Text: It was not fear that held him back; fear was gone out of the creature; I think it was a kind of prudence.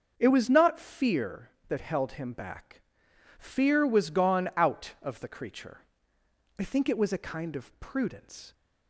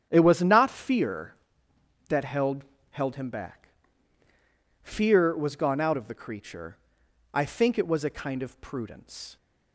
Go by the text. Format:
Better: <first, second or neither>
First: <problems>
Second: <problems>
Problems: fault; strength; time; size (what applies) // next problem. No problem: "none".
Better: first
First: starts louder than the rest; until 1.2 s; 6.5 dB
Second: starts louder than the rest; strong; until 1.1 s; 9 dB // says "held" twice; at 2.9 s